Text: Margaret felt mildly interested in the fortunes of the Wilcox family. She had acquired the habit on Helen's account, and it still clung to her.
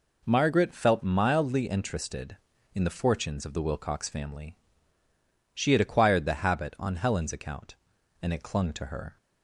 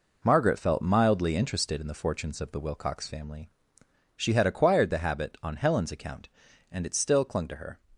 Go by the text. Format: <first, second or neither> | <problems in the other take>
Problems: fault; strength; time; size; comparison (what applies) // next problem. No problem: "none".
second | skips "still"; at 8.4 s